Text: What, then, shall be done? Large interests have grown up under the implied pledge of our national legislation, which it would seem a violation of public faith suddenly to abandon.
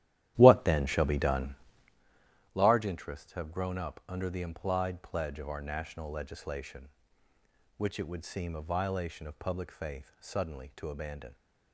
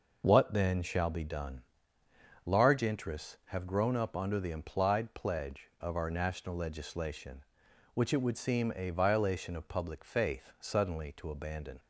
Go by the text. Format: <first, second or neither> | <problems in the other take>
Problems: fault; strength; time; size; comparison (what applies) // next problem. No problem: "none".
second | starts louder than the rest; strong; until 2.0 s; 13 dB